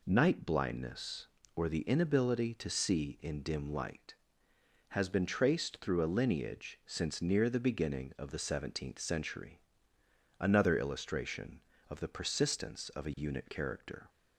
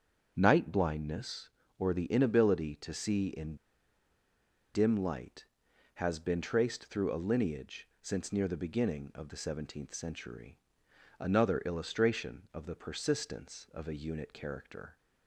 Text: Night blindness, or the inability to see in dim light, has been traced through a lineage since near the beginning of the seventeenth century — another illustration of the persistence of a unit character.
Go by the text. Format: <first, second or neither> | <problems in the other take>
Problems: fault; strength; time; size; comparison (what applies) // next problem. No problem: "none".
first | starts louder than the rest; strong; until 1.3 s; 7 dB // pauses between "in" and "dim"; at 3.5 s; 1.1 s long // pauses between "lineage" and "since"; slight; at 7.8 s; 0.16 s long